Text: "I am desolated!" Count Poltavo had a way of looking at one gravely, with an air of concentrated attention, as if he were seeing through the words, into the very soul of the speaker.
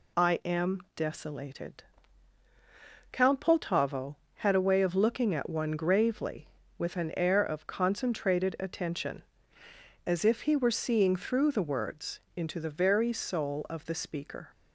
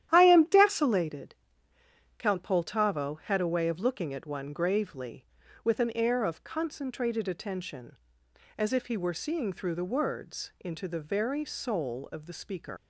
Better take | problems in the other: first | starts louder than the rest; strong; until 1.1 s; 11.5 dB // leaves "speaker" unfinished; at 12.7 s; 90 ms

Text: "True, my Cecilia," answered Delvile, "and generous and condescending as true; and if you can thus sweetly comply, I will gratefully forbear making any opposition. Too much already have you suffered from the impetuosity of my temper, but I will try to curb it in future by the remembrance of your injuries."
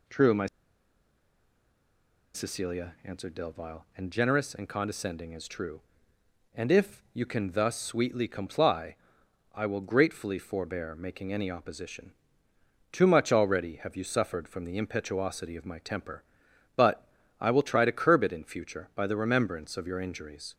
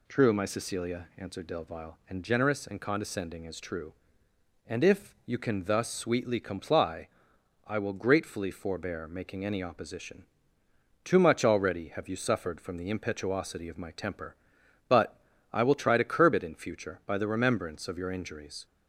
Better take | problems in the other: second | pauses between "my" and "Cecilia"; strong; at 0.4 s; 1.8 s long // pauses between "but" and "I"; slight; at 17.0 s; 0.34 s long; slight in the second

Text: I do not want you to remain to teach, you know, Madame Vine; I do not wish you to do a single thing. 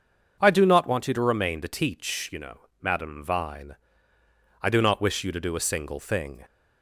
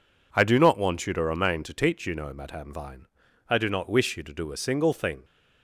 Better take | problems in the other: neither | none

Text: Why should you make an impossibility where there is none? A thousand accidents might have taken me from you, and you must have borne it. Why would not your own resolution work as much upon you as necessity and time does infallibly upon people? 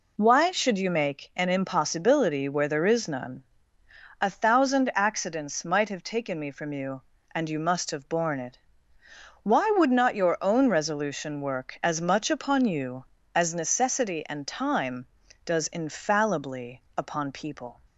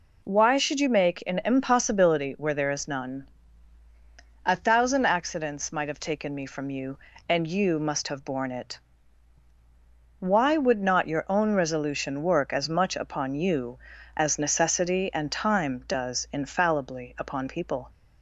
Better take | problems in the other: neither | none

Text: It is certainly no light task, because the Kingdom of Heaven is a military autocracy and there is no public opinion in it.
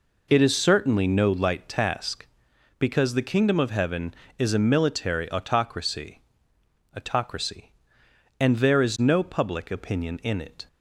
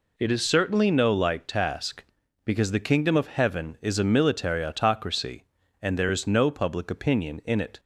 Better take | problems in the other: second | says "autocracy" twice; at 6.9 s

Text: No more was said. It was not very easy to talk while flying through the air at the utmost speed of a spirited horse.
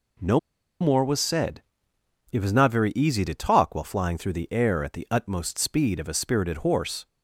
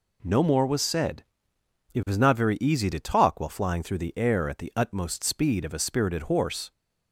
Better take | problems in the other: second | pauses between "No" and "more"; at 0.3 s; 0.41 s long

